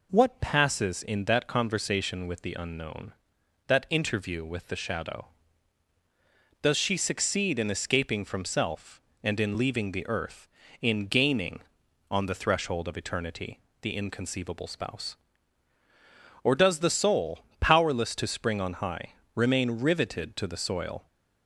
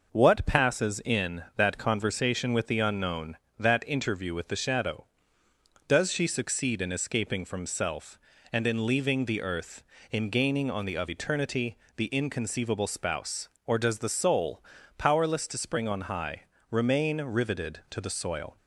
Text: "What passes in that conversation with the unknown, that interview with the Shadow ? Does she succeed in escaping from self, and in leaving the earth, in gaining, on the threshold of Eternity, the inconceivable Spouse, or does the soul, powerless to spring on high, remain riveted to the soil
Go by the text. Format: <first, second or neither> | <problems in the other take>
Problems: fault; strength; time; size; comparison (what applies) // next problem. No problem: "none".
first | skips "threshold"; at 10.9 s